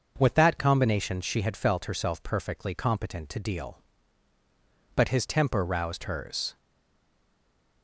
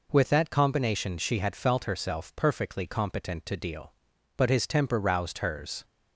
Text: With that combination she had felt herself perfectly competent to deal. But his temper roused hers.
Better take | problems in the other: second | starts louder than the rest; until 1.1 s; 6.5 dB // stays silent after the last word; noticeable; from 6.5 s on; 1.3 s long

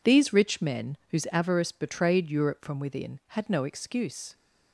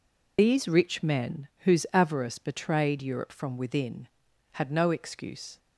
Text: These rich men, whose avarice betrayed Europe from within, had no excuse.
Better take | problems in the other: first | loses the start of "These"; at 0.3 s; 40 ms

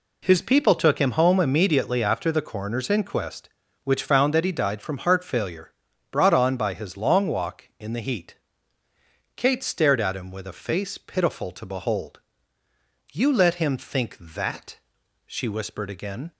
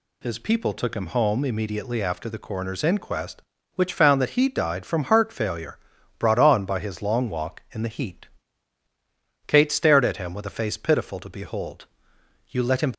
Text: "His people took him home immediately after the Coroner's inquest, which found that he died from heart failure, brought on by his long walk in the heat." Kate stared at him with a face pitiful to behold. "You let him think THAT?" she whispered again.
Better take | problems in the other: first | stops before "think THAT she whispered again"; at 12.9 s

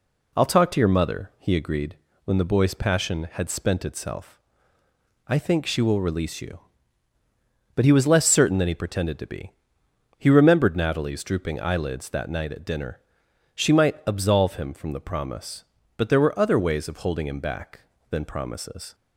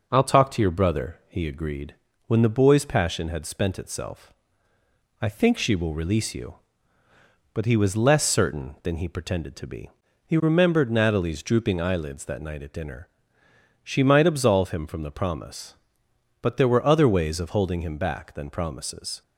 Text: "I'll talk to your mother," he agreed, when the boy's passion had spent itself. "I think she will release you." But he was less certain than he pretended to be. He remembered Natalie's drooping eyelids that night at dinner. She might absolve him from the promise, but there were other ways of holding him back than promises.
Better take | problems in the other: first | says "brother" for "mother"; at 0.7 s

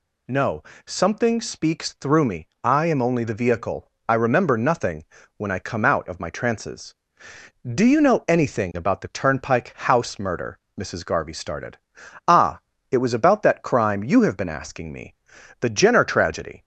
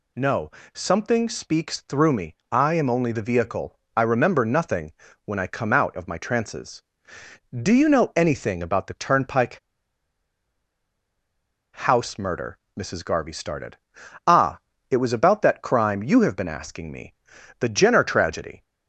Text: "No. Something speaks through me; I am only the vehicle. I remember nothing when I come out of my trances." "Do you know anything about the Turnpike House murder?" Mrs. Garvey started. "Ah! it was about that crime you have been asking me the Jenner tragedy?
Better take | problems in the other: first | pauses between "nothing" and "when"; slight; at 4.9 s; 0.32 s long; slight in the first // pauses between "Turnpike" and "House"; strong; at 9.5 s; 2.1 s long // pauses between "me" and "the"; noticeable; at 17.1 s; 0.46 s long; noticeable in the first

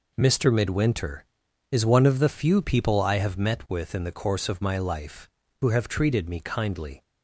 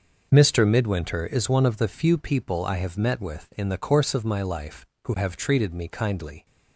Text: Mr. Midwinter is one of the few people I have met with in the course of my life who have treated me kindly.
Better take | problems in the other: neither | none

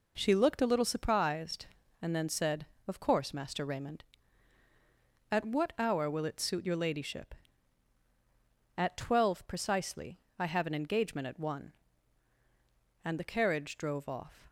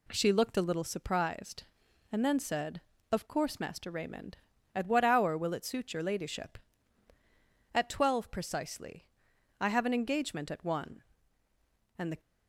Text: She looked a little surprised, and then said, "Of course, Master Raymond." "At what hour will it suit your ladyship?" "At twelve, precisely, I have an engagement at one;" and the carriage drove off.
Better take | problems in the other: first | stops before "carriage drove off"; at 12.2 s

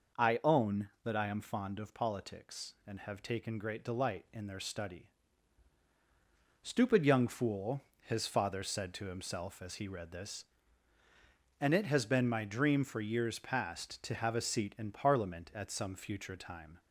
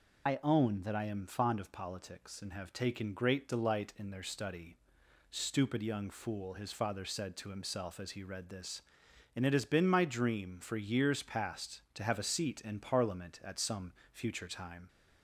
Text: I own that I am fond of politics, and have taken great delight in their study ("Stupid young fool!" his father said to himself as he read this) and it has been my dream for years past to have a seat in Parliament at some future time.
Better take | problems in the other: first | loses the start of "I"; at 0.2 s; 40 ms // pauses between "some" and "future"; slight; at 13.9 s; 0.22 s long

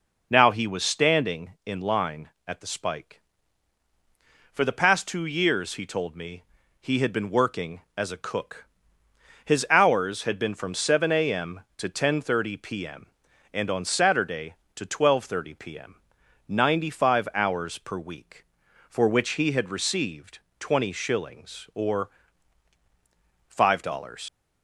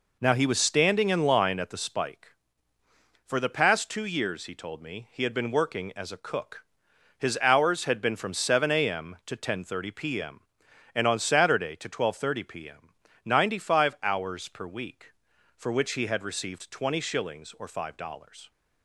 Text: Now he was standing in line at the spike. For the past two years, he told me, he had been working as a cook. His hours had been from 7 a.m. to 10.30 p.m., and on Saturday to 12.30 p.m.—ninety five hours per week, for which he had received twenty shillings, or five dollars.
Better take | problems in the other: second | pauses between "received" and "twenty"; slight; at 20.3 s; 0.20 s long // pauses between "or" and "five"; strong; at 22.0 s; 1.3 s long // leaves "dollars" unfinished; at 24.2 s; 95 ms

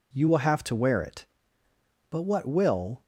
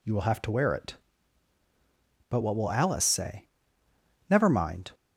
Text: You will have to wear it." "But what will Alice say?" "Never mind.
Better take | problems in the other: second | stops before "Alice say Never mind"; at 3.0 s

